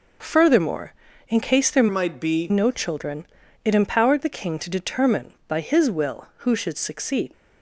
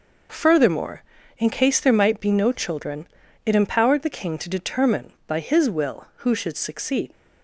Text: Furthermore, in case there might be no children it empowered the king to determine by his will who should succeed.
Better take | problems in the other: second | changes voice from "might" to "be"; from 1.8 to 2.4 s; 0.6 s long // pauses between "children" and "it"; at 3.2 s; 0.40 s long; also in the second

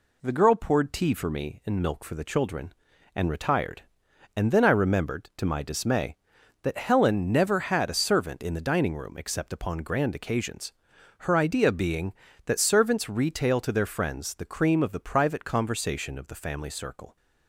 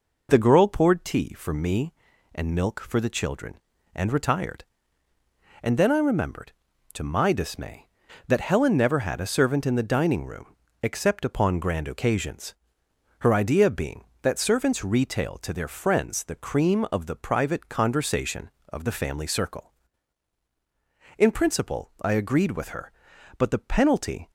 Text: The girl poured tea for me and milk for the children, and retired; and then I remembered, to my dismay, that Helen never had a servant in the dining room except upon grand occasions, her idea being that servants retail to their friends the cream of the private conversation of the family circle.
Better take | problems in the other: first | pauses between "room" and "except"; slight; at 10.5 s; 0.30 s long // goes on to say "In principle I agreed with her but the penalty"; strong; from 21.1 s on; 3.1 s long

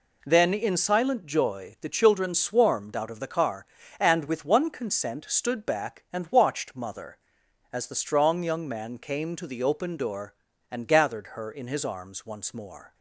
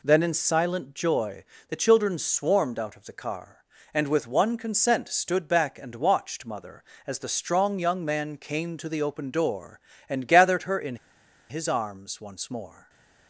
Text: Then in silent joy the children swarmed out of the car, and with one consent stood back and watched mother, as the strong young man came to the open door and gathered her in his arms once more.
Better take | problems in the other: first | pauses between "joy" and "the"; slight; at 1.4 s; 0.24 s long // pauses between "in" and "his"; noticeable; at 10.9 s; 0.53 s long // stays silent after the last word; slight; from 12.7 s on; 0.5 s long

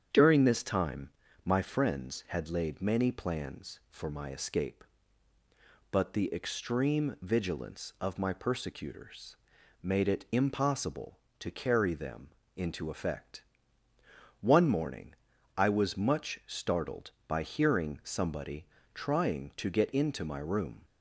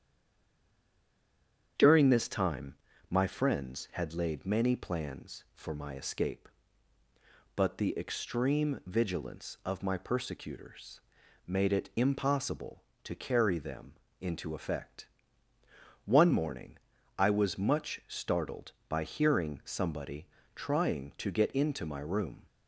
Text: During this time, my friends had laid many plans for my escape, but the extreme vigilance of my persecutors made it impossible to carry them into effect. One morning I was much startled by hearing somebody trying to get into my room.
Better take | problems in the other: first | stays silent before the first word; noticeable; until 1.7 s; 1.7 s long // starts louder than the rest; strong; until 3.1 s; 8 dB; strong in the first // pauses between "persecutors" and "made"; noticeable; at 11.0 s; 0.46 s long; noticeable in the first // pauses between "them" and "into"; slight; at 13.9 s; 0.28 s long; slight in the first // pauses between "morning" and "I"; at 16.7 s; 0.40 s long; also in the first // pauses between "somebody" and "trying"; slight; at 20.2 s; 0.28 s long; slight in the first

